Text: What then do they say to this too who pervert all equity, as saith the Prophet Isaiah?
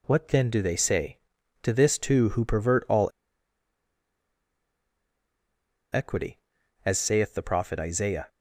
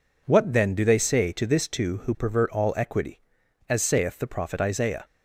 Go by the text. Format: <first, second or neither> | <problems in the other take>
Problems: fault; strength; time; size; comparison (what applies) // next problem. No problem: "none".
second | pauses between "all" and "equity"; strong; at 3.0 s; 2.8 s long